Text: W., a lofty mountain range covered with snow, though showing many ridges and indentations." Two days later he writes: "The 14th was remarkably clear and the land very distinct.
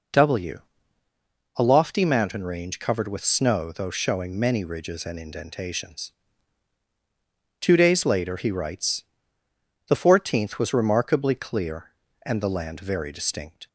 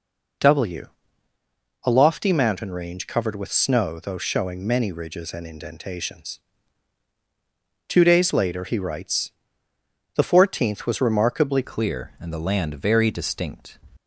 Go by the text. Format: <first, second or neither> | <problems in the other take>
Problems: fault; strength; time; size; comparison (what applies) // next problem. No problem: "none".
first | changes voice at "clear"; from 11.6 s on; 2.1 s long